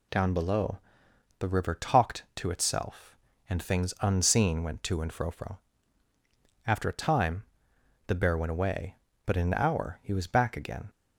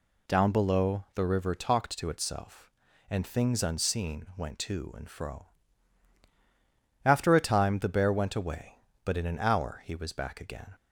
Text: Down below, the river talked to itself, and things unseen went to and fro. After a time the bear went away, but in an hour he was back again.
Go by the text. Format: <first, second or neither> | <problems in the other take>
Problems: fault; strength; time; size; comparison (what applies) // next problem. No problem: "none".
second | says "fro" twice; at 5.2 s // pauses between "time" and "the"; noticeable; at 7.4 s; 0.64 s long